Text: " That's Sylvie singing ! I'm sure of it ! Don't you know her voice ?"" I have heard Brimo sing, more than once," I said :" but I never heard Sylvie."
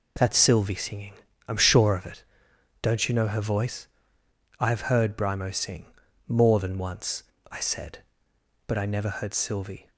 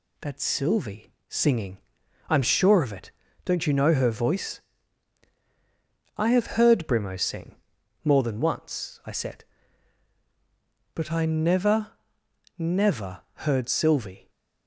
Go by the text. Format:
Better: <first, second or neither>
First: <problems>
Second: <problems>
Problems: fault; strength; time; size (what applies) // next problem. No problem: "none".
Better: first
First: none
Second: pauses between "Sylvie" and "singing"; slight; at 1.1 s; 0.16 s long // says "never" twice; at 12.5 s